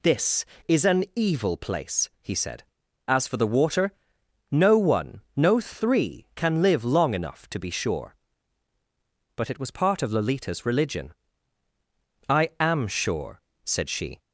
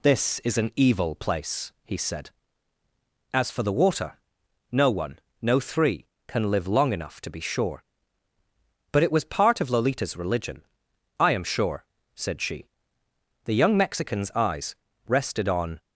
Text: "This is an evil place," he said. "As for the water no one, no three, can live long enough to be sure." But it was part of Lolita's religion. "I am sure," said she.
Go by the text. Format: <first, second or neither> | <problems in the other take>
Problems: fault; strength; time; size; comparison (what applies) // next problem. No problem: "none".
first | pauses between "water" and "no"; noticeable; at 4.1 s; 0.54 s long; noticeable in the first // goes on to say "The young Mexican's eyes rested on"; strong; from 13.4 s on; 2.3 s long